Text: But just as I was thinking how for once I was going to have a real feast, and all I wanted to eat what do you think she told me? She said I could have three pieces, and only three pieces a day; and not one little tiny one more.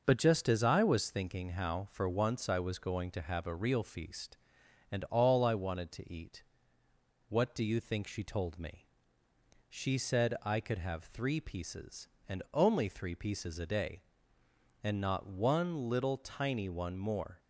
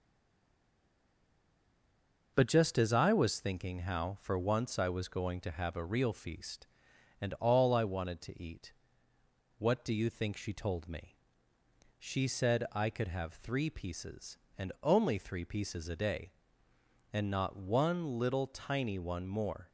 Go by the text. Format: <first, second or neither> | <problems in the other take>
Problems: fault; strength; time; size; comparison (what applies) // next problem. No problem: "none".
first | stays silent before the first word; until 2.3 s; 2.3 s long // pauses between "eat" and "what"; noticeable; at 8.7 s; 0.84 s long; noticeable in the first